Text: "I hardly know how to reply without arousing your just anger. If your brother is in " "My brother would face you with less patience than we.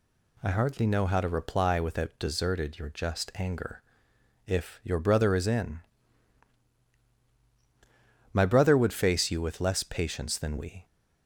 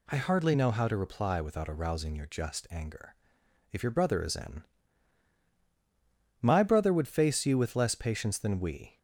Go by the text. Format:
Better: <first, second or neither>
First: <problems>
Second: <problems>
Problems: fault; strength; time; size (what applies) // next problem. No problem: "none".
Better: second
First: says "deserted" for "arousing"; at 2.1 s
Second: none